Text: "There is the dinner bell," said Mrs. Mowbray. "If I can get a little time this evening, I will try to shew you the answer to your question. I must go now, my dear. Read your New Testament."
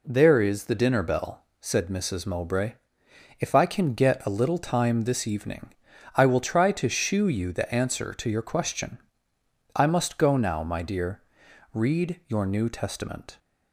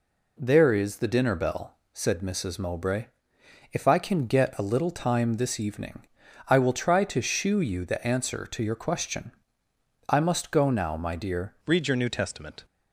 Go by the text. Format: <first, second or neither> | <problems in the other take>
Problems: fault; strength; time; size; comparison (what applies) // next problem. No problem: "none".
first | changes voice at "Read"; from 11.6 s on; 1.0 s long